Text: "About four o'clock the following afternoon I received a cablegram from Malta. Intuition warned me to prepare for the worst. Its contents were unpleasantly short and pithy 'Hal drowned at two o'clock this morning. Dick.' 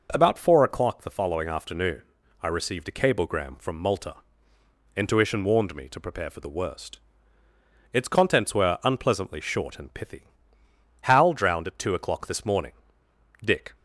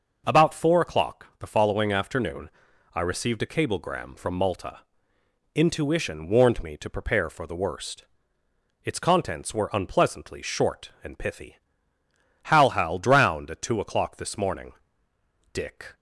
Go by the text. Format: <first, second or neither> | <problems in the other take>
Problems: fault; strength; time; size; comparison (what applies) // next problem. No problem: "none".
first | pauses between "afternoon" and "I"; noticeable; at 2.4 s; 0.46 s long; also in the first // pauses between "pithy" and "Hal"; noticeable; at 11.5 s; 0.86 s long; noticeable in the first // says "Hal" twice; at 12.7 s